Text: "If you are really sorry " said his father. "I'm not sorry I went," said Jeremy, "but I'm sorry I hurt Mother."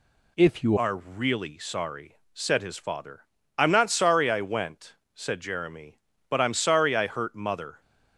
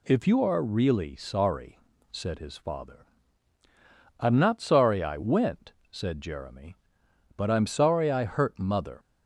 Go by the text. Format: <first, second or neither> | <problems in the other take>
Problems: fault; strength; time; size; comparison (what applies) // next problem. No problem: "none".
second | changes voice at "are"; from 0.7 s on; 7.1 s long